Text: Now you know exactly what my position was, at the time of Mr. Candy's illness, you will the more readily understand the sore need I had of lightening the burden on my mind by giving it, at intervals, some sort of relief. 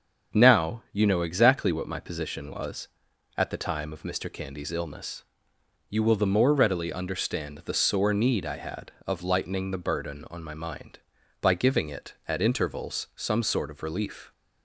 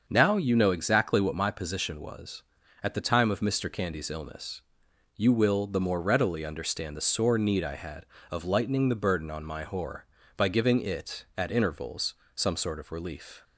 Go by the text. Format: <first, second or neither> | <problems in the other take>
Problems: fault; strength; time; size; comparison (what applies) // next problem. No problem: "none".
first | starts louder than the rest; until 1.0 s; 6.5 dB; strong in the first // says "whore" for "mind"; at 9.6 s